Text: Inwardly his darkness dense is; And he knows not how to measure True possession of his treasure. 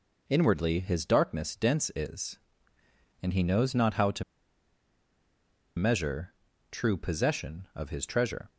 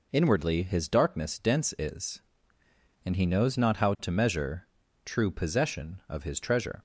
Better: second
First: pauses between "to" and "measure"; strong; at 4.2 s; 1.5 s long // pauses between "measure" and "True"; at 6.3 s; 0.38 s long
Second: pauses between "measure" and "True"; at 4.6 s; 0.38 s long

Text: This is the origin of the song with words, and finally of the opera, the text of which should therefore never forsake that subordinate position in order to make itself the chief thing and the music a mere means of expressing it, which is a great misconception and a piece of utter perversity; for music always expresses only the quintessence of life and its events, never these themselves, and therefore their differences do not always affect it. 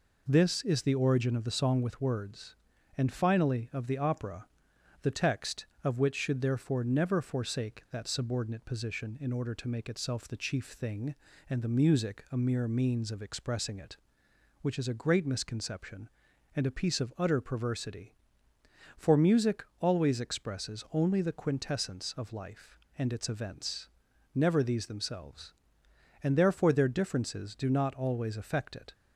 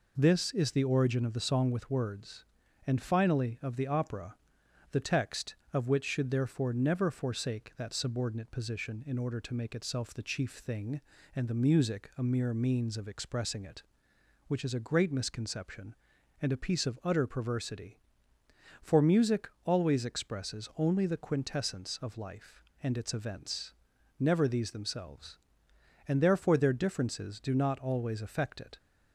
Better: neither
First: pauses between "music" and "always"; slight; at 19.6 s; 0.16 s long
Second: pauses between "music" and "always"; slight; at 19.4 s; 0.16 s long

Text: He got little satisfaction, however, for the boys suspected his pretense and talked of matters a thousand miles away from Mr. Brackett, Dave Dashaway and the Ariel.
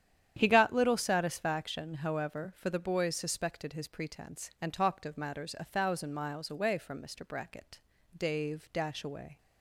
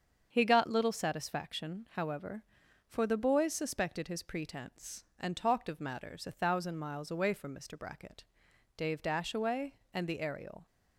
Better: second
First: starts louder than the rest; strong; until 1.3 s; 9.5 dB // stops before "and the Ariel"; at 9.3 s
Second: starts louder than the rest; strong; until 1.3 s; 7 dB

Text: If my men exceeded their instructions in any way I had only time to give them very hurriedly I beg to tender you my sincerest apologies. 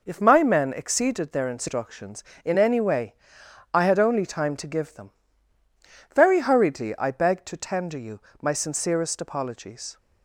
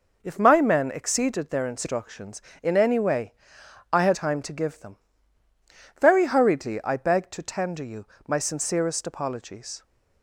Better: first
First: pauses between "way" and "I"; noticeable; at 3.1 s; 0.60 s long // pauses between "them" and "very"; at 5.1 s; 1.0 s long // pauses between "you" and "my"; slight; at 8.1 s; 0.22 s long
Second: pauses between "way" and "I"; noticeable; at 3.3 s; 0.60 s long // skips "only"; at 4.1 s // pauses between "them" and "very"; at 4.9 s; 1.0 s long // pauses between "you" and "my"; slight; at 8.0 s; 0.22 s long

